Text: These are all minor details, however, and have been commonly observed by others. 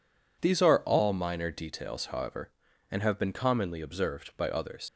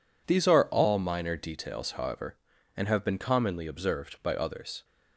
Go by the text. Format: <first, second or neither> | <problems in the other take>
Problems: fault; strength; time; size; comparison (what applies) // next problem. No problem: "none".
second | leaves "others" unfinished; at 4.8 s; 100 ms